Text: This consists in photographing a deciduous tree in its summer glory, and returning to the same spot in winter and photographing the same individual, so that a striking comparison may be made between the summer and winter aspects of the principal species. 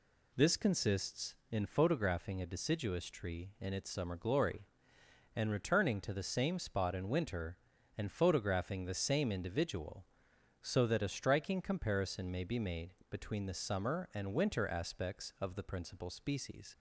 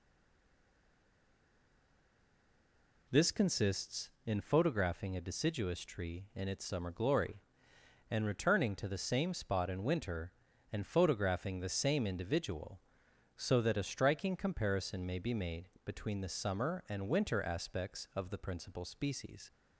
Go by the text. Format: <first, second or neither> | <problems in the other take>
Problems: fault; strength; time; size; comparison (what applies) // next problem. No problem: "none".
first | stays silent before the first word; strong; until 3.0 s; 3.0 s long // pauses between "made" and "between"; slight; at 15.6 s; 0.16 s long; slight in the first